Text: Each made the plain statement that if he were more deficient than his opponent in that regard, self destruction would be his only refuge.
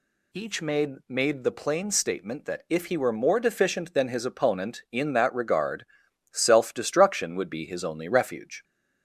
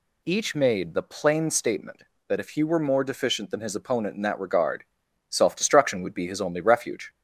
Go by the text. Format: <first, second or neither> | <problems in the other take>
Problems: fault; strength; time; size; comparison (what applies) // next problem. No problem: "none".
second | says "made" twice; at 1.0 s